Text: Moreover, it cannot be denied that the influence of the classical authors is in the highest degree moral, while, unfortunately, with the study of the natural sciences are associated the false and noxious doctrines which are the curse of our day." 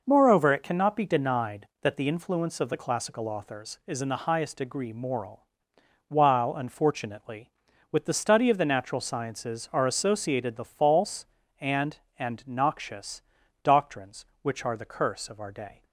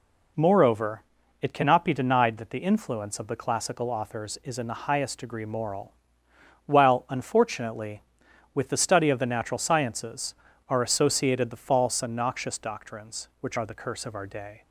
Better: second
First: says "and" twice; at 12.1 s // pauses between "noxious" and "doctrines"; at 13.2 s; 0.40 s long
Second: none

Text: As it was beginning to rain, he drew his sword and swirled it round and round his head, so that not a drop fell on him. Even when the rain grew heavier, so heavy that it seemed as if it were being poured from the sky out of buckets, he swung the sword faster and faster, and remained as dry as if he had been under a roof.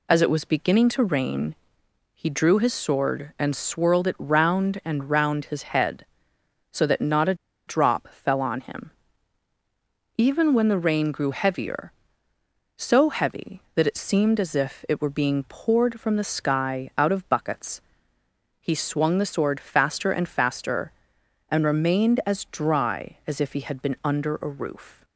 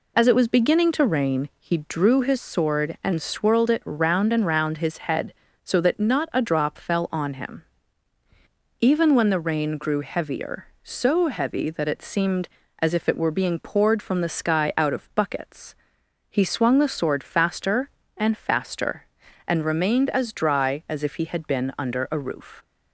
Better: second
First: pauses between "a" and "drop"; slight; at 7.3 s; 0.33 s long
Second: none

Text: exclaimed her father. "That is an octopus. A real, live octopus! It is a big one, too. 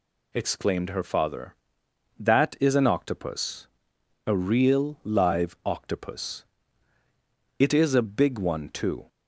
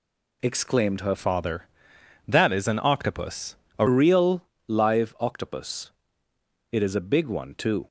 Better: first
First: none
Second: changes voice from "father" to "A"; from 1.1 to 3.8 s; 2.7 s long

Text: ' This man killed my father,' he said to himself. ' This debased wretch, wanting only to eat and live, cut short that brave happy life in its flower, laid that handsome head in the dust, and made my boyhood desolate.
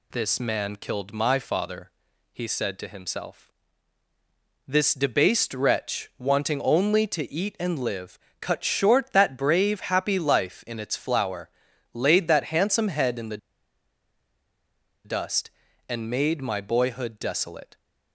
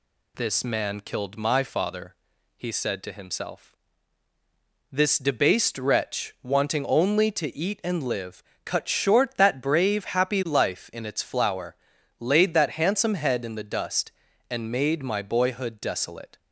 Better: second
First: pauses between "the" and "dust"; strong; at 13.3 s; 1.6 s long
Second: none

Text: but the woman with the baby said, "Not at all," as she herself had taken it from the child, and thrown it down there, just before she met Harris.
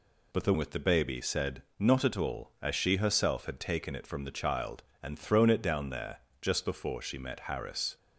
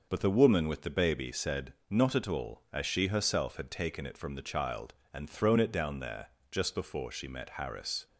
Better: second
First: skips "woman"; at 0.5 s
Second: none

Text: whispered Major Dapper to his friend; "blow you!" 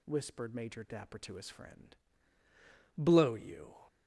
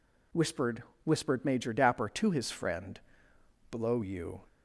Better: first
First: none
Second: says "whispered" twice; at 1.0 s

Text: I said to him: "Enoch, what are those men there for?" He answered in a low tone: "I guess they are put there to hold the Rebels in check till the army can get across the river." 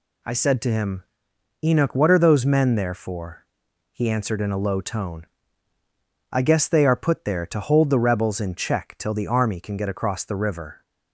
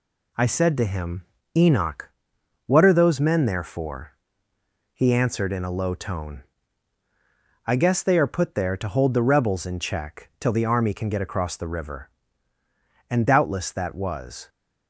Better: first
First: none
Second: goes on to say "And doubtless that was"; from 13.1 s on; 1.3 s long

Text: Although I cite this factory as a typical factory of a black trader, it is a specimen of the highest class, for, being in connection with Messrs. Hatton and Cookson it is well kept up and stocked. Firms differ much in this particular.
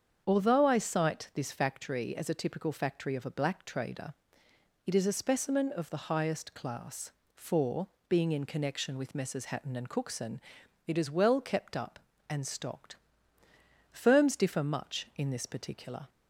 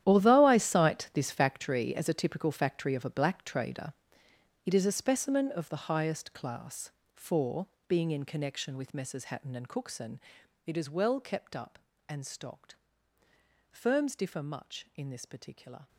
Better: first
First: starts louder than the rest; strong; until 1.2 s; 7.5 dB // pauses between "Cookson" and "it"; noticeable; at 10.3 s; 0.48 s long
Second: gets quieter; strong; throughout; 16 dB // starts louder than the rest; strong; until 1.0 s; 11 dB // pauses between "Cookson" and "it"; noticeable; at 10.1 s; 0.48 s long

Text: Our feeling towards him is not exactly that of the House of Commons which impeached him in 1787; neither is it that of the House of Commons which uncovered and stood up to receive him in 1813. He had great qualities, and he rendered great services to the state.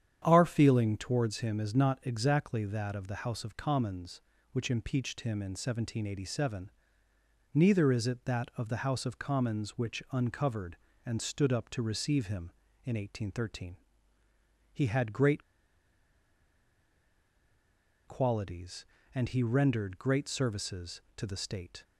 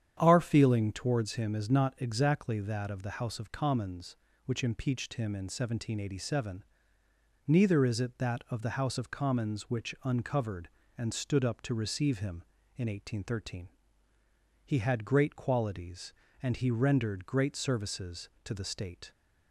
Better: second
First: starts louder than the rest; strong; until 1.2 s; 9 dB // pauses between "great" and "qualities"; strong; at 15.4 s; 2.6 s long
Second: starts louder than the rest; strong; until 1.2 s; 9 dB

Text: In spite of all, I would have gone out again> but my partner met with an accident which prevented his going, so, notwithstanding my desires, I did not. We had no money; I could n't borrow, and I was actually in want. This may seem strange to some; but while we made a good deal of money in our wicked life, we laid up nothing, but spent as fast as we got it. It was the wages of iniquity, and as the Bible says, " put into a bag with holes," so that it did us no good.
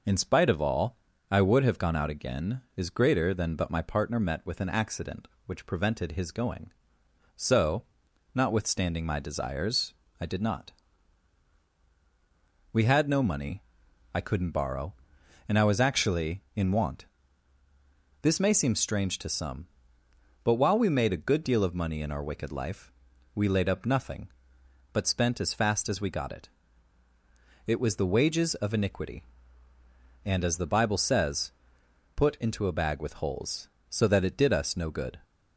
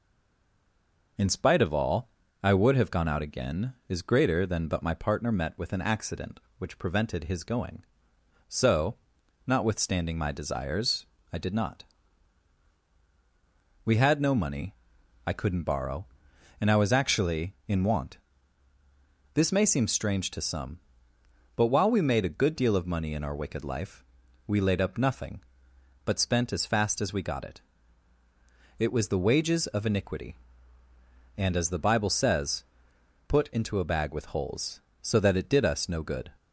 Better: first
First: none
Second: stays silent before the first word; until 1.1 s; 1.1 s long

